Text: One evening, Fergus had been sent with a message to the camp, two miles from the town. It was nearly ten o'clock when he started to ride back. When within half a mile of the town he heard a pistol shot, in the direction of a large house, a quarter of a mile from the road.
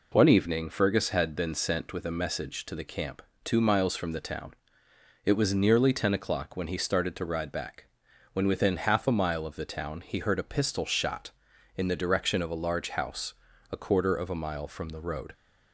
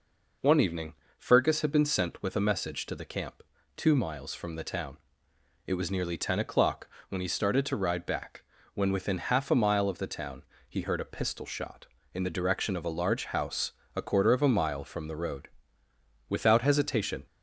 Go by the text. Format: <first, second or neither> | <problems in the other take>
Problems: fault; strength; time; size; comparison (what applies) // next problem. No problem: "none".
first | pauses between "o'clock" and "when"; slight; at 6.8 s; 0.22 s long // pauses between "town" and "he"; slight; at 10.4 s; 0.26 s long // goes on to say "Without hesitation"; noticeable; from 16.2 s on; 0.96 s long